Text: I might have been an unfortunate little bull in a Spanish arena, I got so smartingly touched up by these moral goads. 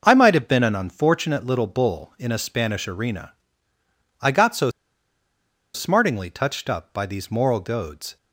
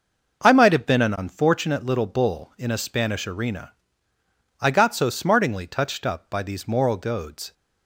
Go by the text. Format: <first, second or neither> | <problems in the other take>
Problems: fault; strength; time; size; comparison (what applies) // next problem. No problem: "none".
second | pauses between "so" and "smartingly"; at 4.7 s; 1.0 s long